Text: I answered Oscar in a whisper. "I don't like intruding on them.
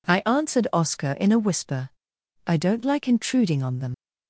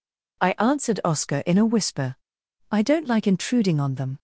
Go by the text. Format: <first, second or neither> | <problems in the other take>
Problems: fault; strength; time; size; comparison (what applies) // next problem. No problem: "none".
second | leaves "them" unfinished; at 3.9 s; 85 ms